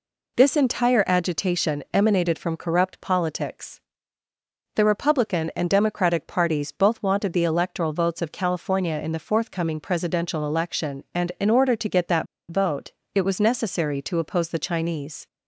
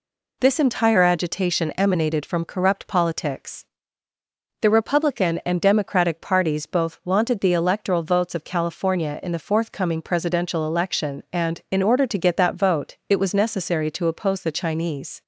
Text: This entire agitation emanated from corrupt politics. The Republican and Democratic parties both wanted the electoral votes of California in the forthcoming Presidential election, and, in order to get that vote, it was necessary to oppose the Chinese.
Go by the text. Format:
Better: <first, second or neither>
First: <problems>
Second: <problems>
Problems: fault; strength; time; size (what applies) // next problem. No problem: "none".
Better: second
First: pauses between "that" and "vote"; slight; at 12.2 s; 0.24 s long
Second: none